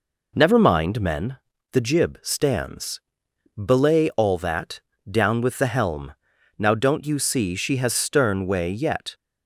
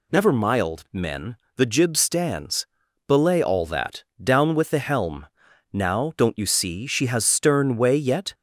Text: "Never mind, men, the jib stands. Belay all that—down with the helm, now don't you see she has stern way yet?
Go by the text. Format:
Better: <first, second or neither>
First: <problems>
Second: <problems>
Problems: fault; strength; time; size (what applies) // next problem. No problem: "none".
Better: first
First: none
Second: says "mild" for "mind"; at 0.3 s